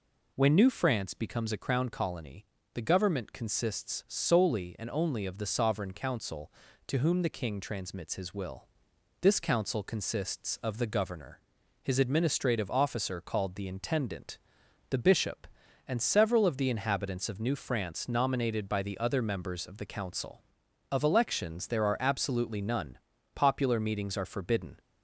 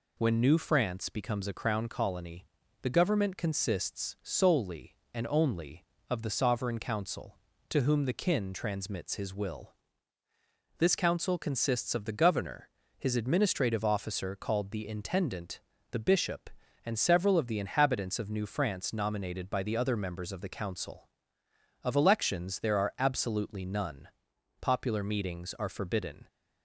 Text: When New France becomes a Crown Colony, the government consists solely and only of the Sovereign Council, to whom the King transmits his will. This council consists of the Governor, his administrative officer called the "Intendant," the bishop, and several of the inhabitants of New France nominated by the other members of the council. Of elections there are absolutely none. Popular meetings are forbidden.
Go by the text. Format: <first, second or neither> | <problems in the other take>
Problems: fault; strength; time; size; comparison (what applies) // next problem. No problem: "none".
first | says "Kin" for "King"; at 8.1 s